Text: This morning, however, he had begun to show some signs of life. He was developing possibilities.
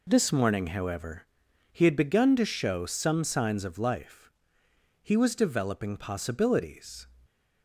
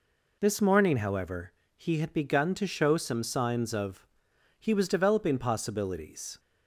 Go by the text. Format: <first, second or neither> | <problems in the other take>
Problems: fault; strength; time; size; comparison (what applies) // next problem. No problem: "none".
first | skips "life"; at 4.3 s